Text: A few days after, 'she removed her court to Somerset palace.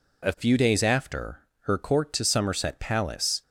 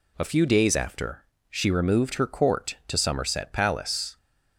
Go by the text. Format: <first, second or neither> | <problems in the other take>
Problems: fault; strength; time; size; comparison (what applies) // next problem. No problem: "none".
second | skips "she removed"; at 1.5 s